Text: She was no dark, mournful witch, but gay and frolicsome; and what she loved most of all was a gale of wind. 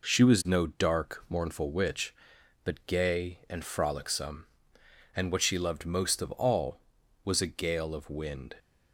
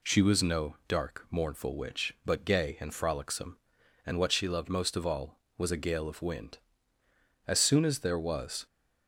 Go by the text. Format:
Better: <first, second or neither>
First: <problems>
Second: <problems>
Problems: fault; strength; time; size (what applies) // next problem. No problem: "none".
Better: first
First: none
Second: goes on to say "As soon as there was"; noticeable; from 7.4 s on; 1.2 s long